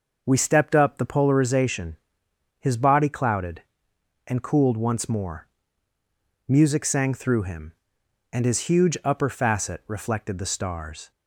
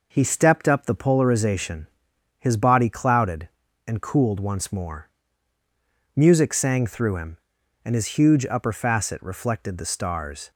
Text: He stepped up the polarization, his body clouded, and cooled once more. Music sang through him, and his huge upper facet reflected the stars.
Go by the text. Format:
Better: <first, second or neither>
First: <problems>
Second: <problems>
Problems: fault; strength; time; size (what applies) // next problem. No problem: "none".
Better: second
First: says "We" for "He"; at 0.2 s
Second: none